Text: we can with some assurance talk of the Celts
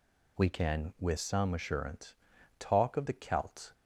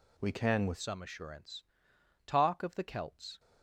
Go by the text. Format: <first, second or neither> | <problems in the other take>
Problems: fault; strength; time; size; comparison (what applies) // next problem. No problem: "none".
first | changes voice at "some"; from 0.7 s on; 2.6 s long // pauses between "assurance" and "talk"; noticeable; at 1.6 s; 0.62 s long; noticeable in the first